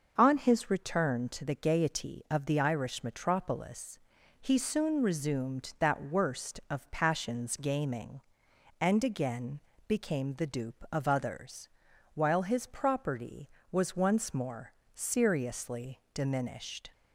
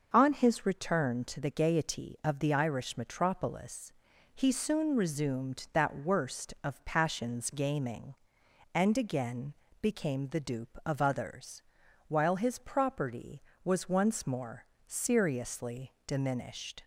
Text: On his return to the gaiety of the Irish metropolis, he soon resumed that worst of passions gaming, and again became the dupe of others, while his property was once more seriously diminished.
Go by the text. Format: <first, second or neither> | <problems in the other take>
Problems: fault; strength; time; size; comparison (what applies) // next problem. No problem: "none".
neither | pauses between "again" and "became"; slight; the same in both // pauses between "more" and "seriously"; slight; the same in both